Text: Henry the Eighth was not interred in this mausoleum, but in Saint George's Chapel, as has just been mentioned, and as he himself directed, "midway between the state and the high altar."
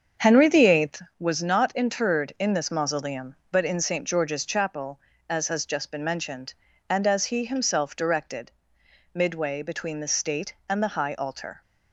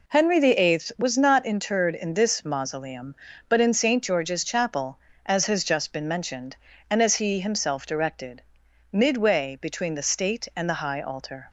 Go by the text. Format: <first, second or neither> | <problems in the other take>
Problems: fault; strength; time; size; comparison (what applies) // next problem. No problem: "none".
second | starts louder than the rest; strong; until 1.2 s; 7 dB